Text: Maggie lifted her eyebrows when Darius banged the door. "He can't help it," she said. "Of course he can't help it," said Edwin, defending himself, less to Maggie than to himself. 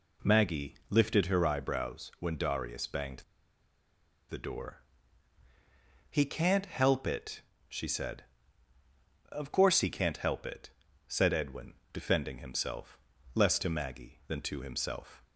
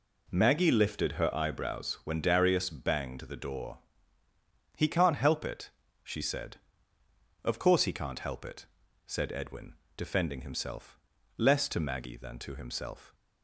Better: second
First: pauses between "Maggie" and "lifted"; slight; at 0.7 s; 0.16 s long // pauses between "banged" and "the"; at 3.2 s; 1.0 s long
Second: none

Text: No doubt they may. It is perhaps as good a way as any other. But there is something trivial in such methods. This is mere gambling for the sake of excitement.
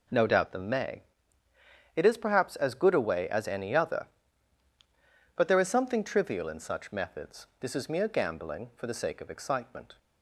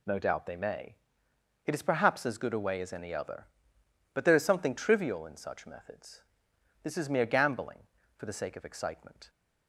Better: second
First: says "them" for "they"; at 0.5 s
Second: none

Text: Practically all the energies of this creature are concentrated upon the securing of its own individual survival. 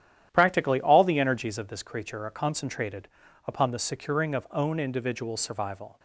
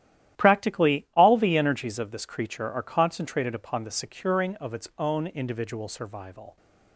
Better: second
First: starts louder than the rest; strong; until 1.3 s; 11 dB // pauses between "concentrated" and "upon"; at 3.0 s; 0.38 s long // skips "its"; at 4.4 s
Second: starts louder than the rest; strong; until 1.4 s; 12.5 dB

